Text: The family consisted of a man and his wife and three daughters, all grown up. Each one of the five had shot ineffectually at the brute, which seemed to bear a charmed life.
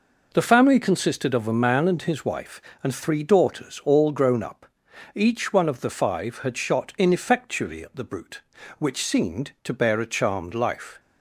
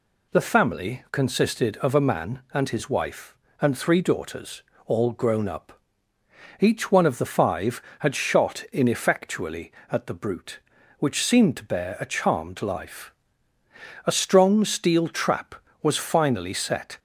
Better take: first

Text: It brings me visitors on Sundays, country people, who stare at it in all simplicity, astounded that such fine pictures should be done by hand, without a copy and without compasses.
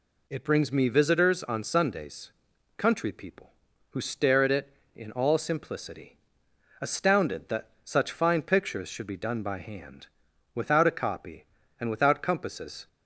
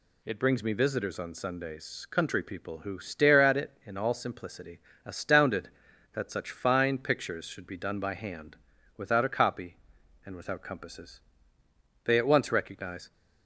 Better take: first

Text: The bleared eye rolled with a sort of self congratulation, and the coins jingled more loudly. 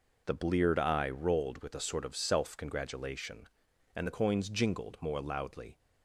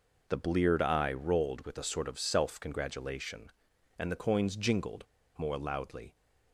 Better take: first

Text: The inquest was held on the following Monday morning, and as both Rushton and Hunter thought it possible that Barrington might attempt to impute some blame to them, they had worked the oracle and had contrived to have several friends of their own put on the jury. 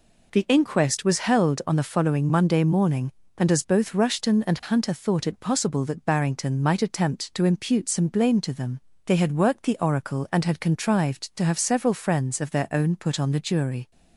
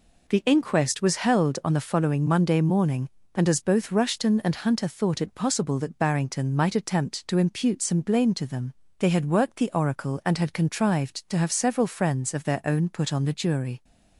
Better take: neither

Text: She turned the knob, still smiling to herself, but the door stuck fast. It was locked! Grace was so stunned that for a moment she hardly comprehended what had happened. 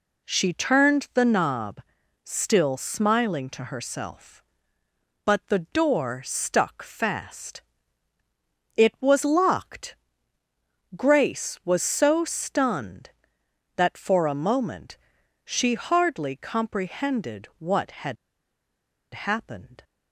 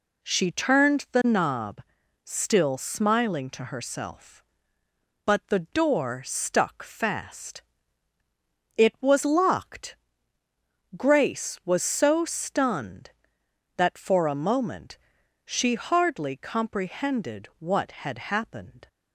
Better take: second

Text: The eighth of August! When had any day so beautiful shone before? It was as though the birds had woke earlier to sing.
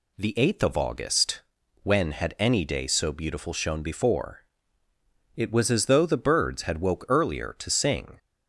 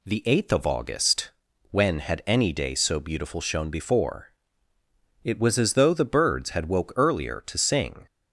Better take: neither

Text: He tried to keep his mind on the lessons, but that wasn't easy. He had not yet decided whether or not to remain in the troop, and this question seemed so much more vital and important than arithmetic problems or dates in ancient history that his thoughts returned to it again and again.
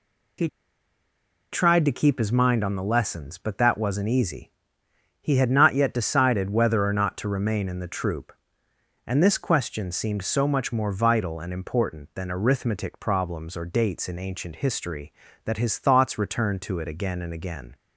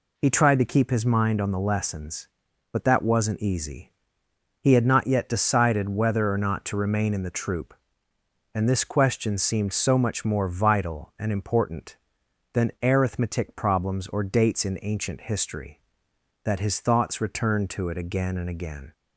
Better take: second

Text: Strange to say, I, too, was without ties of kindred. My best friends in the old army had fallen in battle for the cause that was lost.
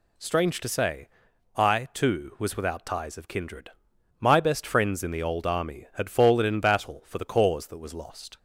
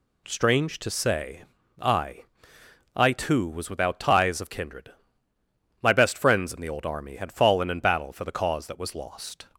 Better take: first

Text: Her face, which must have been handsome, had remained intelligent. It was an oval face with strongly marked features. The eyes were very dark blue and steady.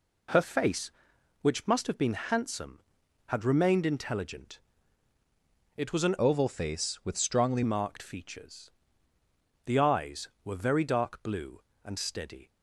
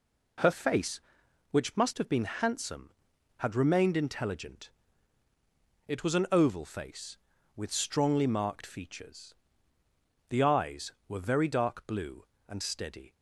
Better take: second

